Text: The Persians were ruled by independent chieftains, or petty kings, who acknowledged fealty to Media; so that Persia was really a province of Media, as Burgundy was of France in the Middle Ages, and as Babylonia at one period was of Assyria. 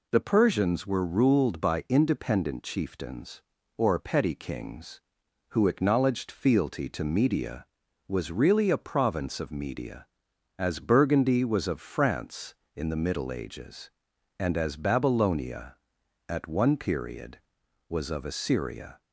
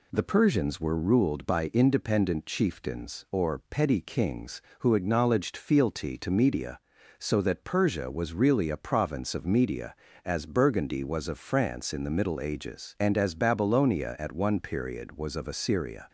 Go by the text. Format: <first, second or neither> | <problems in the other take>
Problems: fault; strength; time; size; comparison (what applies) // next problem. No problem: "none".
second | skips "so that Persia"; at 7.8 s